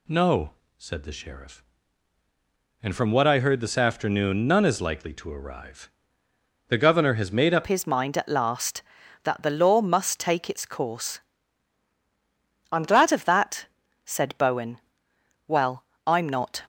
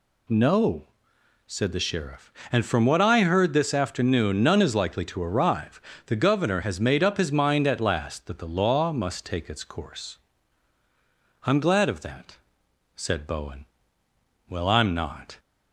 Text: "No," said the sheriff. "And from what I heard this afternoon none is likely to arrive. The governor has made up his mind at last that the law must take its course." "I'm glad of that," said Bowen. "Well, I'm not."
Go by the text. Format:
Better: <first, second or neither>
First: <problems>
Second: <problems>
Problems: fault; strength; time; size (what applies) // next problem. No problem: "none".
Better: second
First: changes voice at "his"; from 7.6 s on; 9.0 s long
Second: none